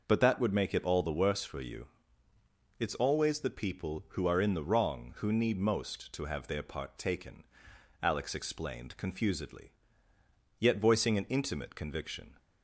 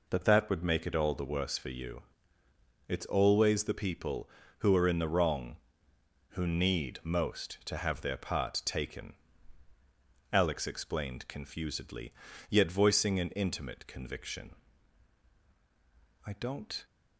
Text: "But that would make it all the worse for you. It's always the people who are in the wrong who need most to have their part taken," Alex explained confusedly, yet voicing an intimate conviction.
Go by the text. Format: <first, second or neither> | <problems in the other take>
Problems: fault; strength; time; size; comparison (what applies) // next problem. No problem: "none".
first | goes on to say "I don't"; from 16.2 s on; 0.60 s long